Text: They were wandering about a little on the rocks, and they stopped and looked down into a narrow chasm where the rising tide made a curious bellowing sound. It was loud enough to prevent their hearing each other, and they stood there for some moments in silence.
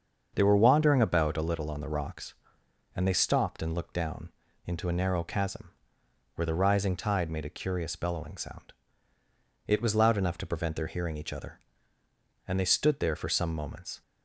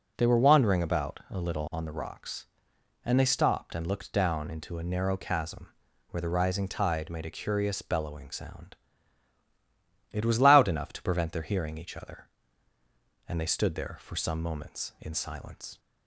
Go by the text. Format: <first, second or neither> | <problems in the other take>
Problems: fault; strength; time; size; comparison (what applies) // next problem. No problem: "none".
second | starts louder than the rest; until 1.3 s; 6.5 dB // pauses between "down" and "into"; slight; at 4.3 s; 0.36 s long // pauses between "chasm" and "where"; noticeable; at 5.7 s; 0.64 s long; also in the second // stops before "in silence"; at 14.0 s